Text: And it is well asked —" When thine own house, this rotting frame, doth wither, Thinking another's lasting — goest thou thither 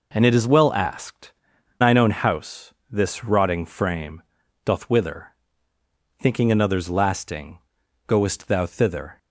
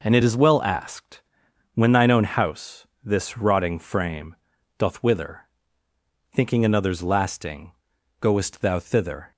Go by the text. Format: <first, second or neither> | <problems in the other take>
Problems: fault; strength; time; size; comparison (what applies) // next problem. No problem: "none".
second | skips "When"; at 1.5 s